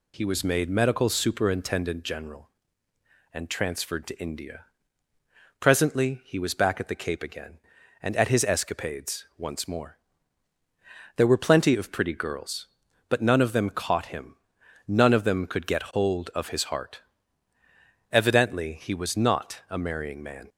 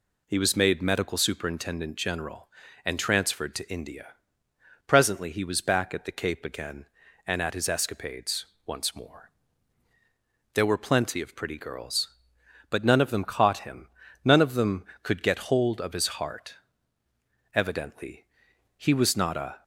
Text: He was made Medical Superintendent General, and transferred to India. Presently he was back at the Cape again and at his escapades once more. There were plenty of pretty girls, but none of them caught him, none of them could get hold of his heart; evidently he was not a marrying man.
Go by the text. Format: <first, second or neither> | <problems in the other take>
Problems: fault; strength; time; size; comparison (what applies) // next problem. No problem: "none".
first | pauses between "escapades" and "once"; slight; at 8.4 s; 0.22 s long // pauses between "evidently" and "he"; noticeable; at 18.2 s; 0.52 s long // stops before "marrying man"; at 19.6 s